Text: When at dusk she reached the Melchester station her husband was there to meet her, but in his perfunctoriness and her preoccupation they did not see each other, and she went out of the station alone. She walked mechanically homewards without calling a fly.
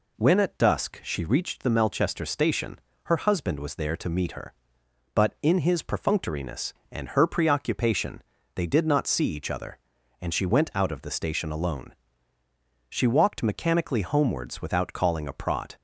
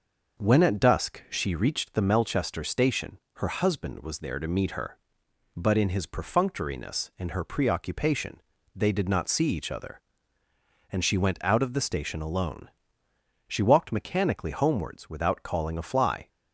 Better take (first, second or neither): second